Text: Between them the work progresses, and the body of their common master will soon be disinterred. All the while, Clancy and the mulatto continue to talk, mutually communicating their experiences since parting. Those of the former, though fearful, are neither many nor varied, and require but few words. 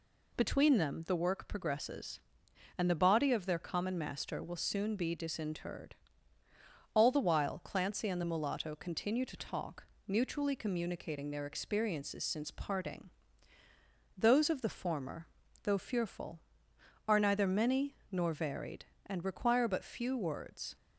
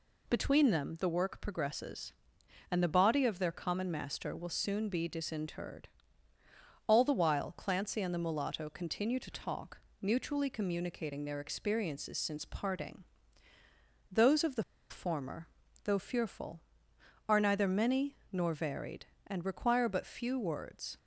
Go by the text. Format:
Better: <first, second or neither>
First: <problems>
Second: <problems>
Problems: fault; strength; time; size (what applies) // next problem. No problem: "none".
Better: first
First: pauses between "many" and "nor"; slight; at 17.9 s; 0.16 s long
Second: pauses between "the" and "former"; slight; at 14.6 s; 0.27 s long // pauses between "many" and "nor"; slight; at 18.1 s; 0.16 s long